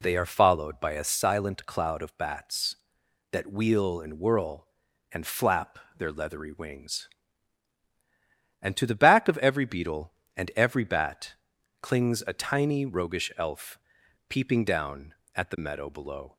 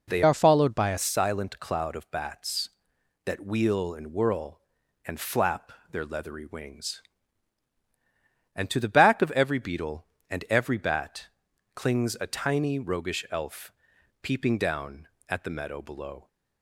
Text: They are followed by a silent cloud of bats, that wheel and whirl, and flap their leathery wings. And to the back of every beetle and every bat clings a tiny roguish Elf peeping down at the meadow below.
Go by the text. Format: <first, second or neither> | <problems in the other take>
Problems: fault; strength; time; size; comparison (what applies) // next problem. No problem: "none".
first | changes voice from "are" to "a"; from 0.2 to 0.9 s; 0.7 s long // pauses between "flap" and "their"; slight; at 5.7 s; 0.18 s long; slight in the first // pauses between "bat" and "clings"; noticeable; at 11.2 s; 0.48 s long; noticeable in the first // pauses between "Elf" and "peeping"; noticeable; at 13.7 s; 0.50 s long; noticeable in the first